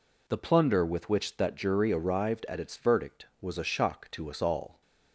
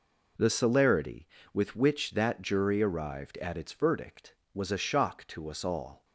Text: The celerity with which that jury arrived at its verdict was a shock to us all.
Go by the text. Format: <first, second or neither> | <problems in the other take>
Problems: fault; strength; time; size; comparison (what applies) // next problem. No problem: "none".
second | says "plunder" for "celerity"; at 0.3 s